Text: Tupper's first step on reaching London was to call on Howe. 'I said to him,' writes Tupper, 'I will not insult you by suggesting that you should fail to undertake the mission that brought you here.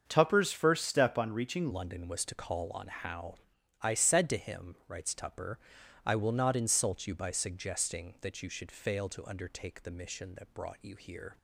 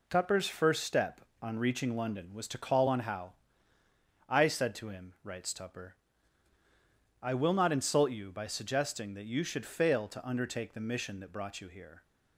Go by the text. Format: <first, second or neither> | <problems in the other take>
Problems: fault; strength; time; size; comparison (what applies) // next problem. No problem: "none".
second | starts louder than the rest; until 1.0 s; 7 dB // changes voice at "London"; from 1.7 s on; 9.6 s long